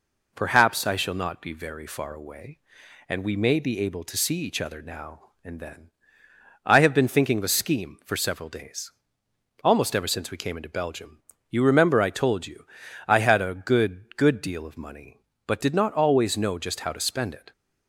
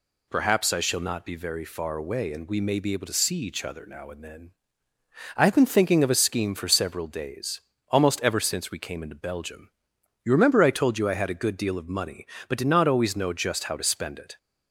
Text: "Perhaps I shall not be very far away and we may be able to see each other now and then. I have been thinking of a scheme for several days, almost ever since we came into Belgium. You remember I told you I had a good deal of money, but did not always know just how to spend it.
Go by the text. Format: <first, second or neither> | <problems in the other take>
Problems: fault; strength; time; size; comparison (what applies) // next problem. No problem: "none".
second | pauses between "you" and "I"; at 12.6 s; 0.40 s long // says "good" twice; at 14.1 s